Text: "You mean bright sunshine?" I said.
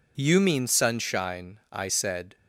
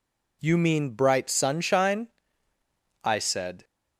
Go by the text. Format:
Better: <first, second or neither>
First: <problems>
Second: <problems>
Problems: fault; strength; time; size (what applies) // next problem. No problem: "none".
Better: second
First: skips "bright"; at 0.6 s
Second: none